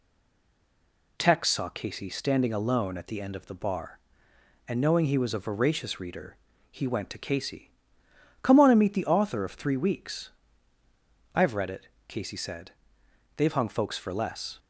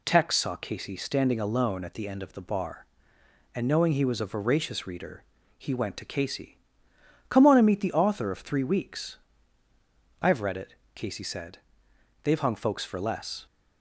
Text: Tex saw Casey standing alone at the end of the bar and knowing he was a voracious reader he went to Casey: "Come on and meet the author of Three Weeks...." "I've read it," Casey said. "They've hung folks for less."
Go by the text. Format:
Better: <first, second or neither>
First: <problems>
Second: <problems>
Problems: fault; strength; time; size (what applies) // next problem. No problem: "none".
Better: second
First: stays silent before the first word; noticeable; until 1.1 s; 1.1 s long // pauses between "reader" and "he"; slight; at 6.3 s; 0.34 s long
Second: pauses between "reader" and "he"; slight; at 5.2 s; 0.34 s long